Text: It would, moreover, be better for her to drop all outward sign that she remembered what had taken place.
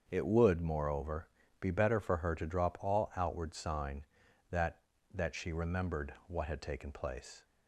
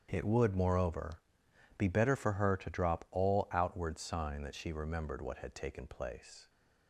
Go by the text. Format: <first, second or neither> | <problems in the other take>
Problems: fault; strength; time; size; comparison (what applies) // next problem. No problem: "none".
second | starts louder than the rest; until 1.1 s; 6.5 dB; strong in the second // says "that" twice; at 5.1 s